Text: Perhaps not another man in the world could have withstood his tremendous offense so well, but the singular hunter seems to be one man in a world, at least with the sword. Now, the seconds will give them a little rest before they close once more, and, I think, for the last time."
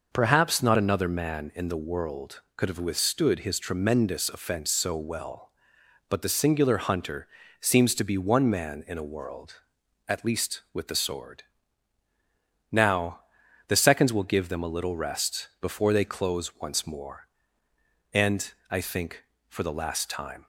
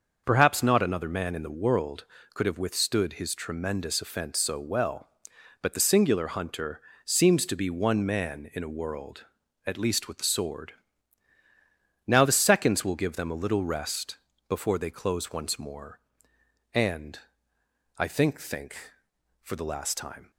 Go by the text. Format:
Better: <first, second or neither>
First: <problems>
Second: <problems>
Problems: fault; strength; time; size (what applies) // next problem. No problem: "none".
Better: first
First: pauses between "hunter" and "seems"; slight; at 7.2 s; 0.32 s long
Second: starts louder than the rest; until 1.2 s; 6.5 dB // pauses between "hunter" and "seems"; slight; at 6.7 s; 0.24 s long // pauses between "rest" and "before"; slight; at 14.1 s; 0.32 s long // says "think" twice; at 18.4 s